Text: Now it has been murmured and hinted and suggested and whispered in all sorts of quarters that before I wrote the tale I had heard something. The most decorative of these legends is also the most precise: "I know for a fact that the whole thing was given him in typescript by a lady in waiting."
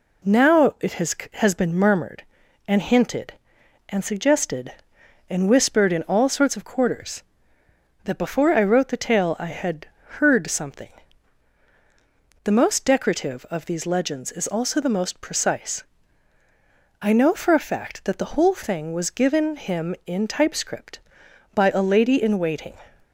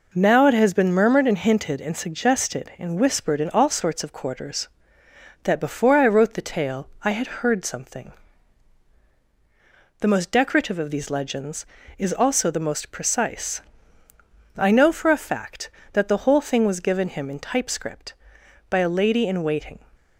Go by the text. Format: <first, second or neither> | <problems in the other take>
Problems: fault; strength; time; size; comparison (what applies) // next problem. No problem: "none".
second | says "has" twice; at 1.3 s // pauses between "had" and "heard"; slight; at 9.8 s; 0.32 s long